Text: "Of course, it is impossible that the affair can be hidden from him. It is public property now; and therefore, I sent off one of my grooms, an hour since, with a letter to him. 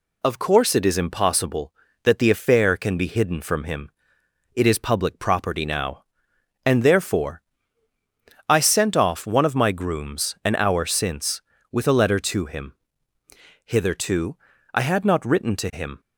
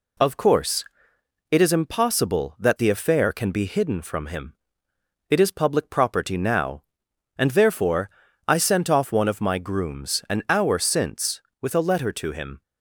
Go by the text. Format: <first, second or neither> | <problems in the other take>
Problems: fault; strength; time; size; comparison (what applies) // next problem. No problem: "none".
second | goes on to say "Hitherto I had not written to him"; strong; from 13.6 s on; 2.3 s long